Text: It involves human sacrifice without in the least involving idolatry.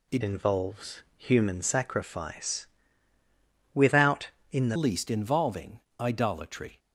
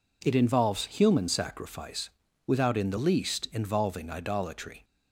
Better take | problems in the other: second | changes voice from "involves" to "the"; from 0.2 to 4.7 s; 4.5 s long // pauses between "involves" and "human"; slight; at 1.0 s; 0.16 s long // pauses between "sacrifice" and "without"; at 2.6 s; 1.0 s long; slight in the second // pauses between "involving" and "idolatry"; slight; at 5.8 s; 0.18 s long

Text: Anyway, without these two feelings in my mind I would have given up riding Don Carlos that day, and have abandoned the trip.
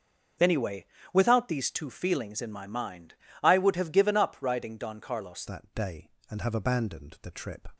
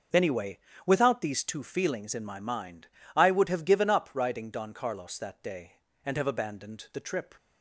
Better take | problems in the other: second | starts louder than the rest; until 1.6 s; 6.5 dB; noticeable in the second // pauses between "mind" and "I"; slight; at 3.1 s; 0.30 s long; slight in the second // changes voice at "that"; from 5.4 s on; 2.2 s long

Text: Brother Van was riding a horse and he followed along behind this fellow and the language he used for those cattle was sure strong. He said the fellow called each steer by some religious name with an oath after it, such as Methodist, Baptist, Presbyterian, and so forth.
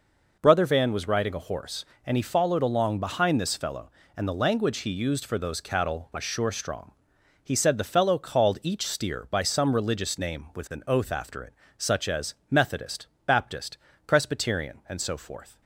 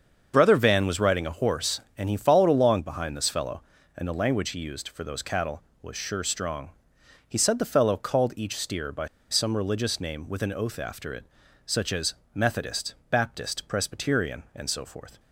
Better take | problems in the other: first | starts louder than the rest; until 1.3 s; 7 dB // pauses between "by" and "some"; slight; at 9.0 s; 0.24 s long // pauses between "as" and "Methodist"; slight; at 12.1 s; 0.18 s long; slight in the first

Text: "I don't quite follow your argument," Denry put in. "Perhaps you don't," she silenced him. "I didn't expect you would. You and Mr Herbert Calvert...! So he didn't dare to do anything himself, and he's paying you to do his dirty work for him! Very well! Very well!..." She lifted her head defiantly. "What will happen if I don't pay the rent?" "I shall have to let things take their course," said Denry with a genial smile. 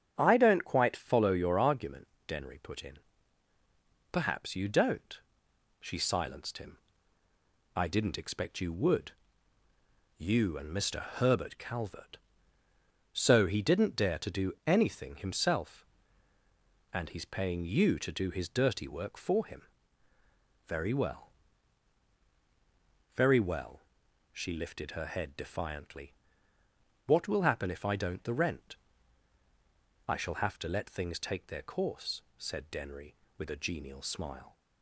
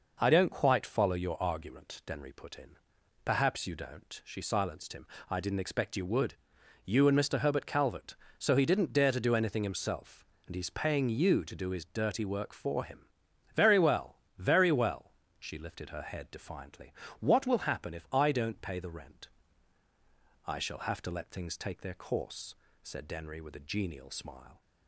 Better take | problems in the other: second | starts louder than the rest; strong; until 1.1 s; 9 dB // skips "pay"; at 28.2 s

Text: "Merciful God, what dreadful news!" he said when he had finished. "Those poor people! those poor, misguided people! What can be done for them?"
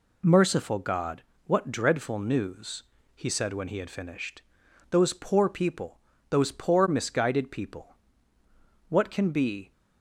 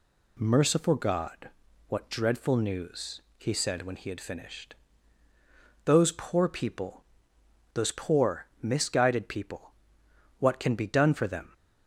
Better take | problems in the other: second | stops before "done for them"; at 9.7 s

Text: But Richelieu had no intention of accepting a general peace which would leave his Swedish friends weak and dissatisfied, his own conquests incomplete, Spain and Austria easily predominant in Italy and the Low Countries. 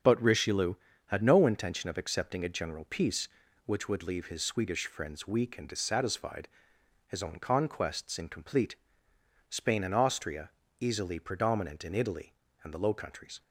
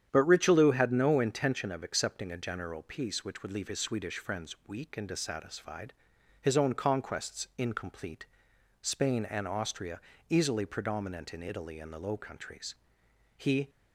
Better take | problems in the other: first | starts louder than the rest; strong; until 1.1 s; 9 dB; also in the first // pauses between "Austria" and "easily"; slight; at 9.9 s; 0.30 s long; slight in the first // goes on to say "He"; slight; from 13.3 s on; 0.32 s long

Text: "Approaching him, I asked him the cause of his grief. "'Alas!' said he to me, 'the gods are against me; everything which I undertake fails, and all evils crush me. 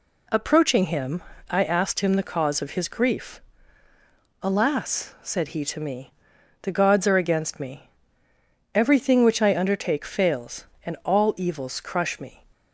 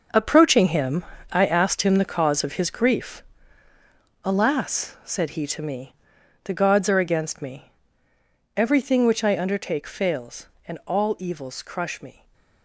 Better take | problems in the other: first | gets quieter; strong; throughout; 10.5 dB // stays silent after the last word; slight; from 12.1 s on; 0.5 s long

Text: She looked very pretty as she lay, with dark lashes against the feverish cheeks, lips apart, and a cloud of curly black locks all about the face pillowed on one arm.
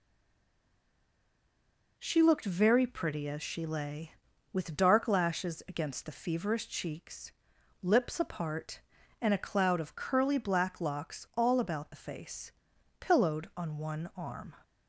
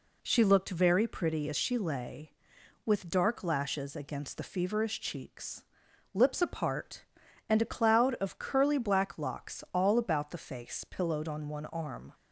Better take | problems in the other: second | stays silent before the first word; noticeable; until 1.9 s; 1.9 s long // pauses between "face" and "pillowed"; noticeable; at 12.5 s; 0.48 s long

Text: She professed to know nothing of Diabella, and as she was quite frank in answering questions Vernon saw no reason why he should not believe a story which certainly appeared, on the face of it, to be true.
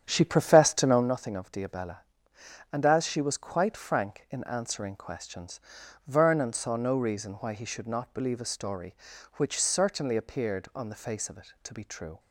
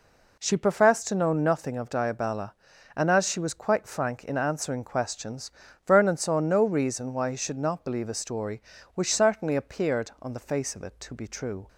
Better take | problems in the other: second | starts louder than the rest; strong; until 1.1 s; 9 dB // pauses between "questions" and "Vernon"; noticeable; at 5.6 s; 0.46 s long; slight in the second

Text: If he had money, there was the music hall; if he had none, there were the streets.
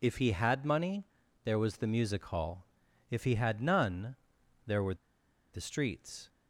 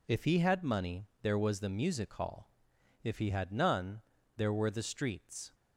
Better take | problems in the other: second | pauses between "were" and "the"; noticeable; at 4.9 s; 0.58 s long

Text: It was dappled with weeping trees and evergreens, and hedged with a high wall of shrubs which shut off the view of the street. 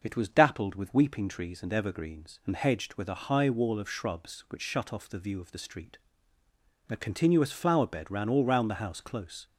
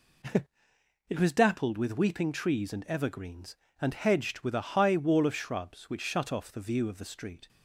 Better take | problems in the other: second | starts louder than the rest; noticeable; until 1.0 s; 6 dB // goes on to say "A continuous flower bed ran all round the house close"; strong; from 6.8 s on; 2.5 s long

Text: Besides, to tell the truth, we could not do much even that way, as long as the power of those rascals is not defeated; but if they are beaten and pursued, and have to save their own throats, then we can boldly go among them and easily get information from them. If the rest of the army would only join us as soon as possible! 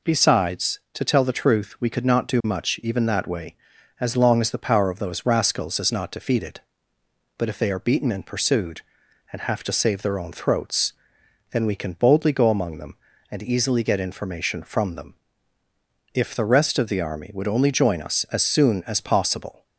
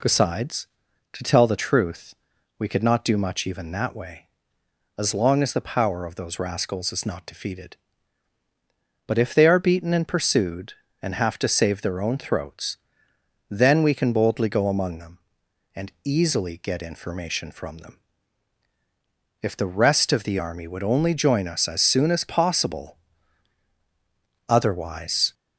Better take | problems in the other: first | goes on to say "Otherwise"; noticeable; from 24.4 s on; 0.86 s long

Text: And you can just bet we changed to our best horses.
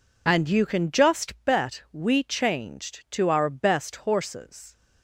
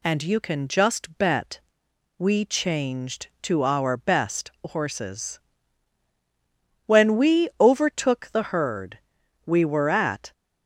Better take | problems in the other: first | pauses between "bet" and "we"; noticeable; at 1.6 s; 0.58 s long // goes on to say "When we overtook the herd we were at"; strong; from 6.8 s on; 3.4 s long

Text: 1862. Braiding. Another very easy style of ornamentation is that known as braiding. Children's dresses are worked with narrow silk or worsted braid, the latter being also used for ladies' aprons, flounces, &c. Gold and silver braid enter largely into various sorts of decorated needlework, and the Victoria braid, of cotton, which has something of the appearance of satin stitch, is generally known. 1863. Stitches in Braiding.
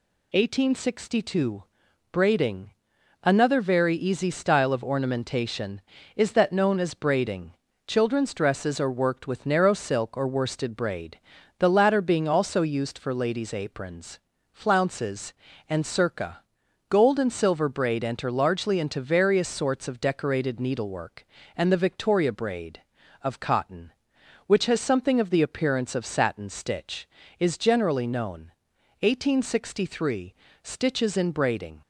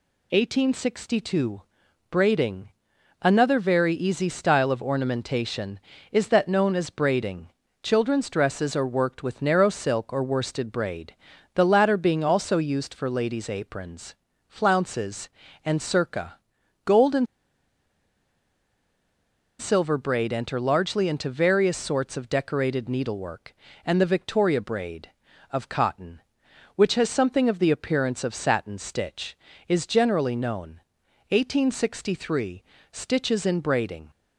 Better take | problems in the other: first | pauses between "and" and "silver"; strong; at 17.2 s; 2.3 s long

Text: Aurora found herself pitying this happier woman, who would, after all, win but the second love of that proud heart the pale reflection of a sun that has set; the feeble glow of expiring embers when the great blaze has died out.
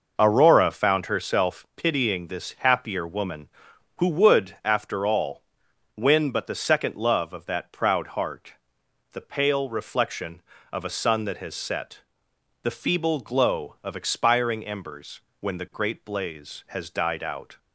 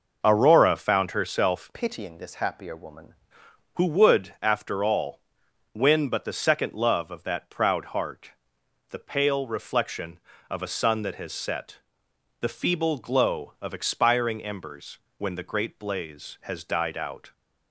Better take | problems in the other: first | changes voice from "pitying" to "woman"; from 1.7 to 3.1 s; 1.4 s long // pauses between "heart" and "the"; noticeable; at 8.3 s; 0.58 s long; noticeable in the first // pauses between "embers" and "when"; slight; at 14.9 s; 0.20 s long; slight in the first

